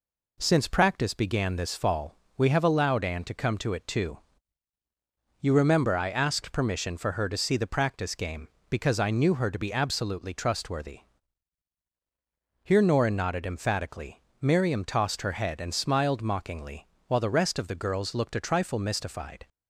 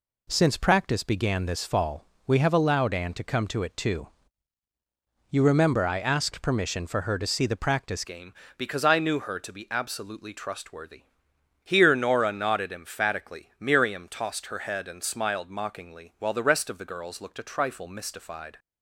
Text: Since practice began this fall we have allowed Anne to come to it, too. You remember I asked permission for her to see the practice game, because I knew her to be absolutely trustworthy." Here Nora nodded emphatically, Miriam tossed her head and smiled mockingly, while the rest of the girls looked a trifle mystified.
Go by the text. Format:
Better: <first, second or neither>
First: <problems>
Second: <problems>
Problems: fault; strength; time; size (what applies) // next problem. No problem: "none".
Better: first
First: pauses between "fall" and "we"; slight; at 2.1 s; 0.22 s long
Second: pauses between "fall" and "we"; slight; at 2.0 s; 0.22 s long // changes voice at "game"; from 8.0 s on; 10.5 s long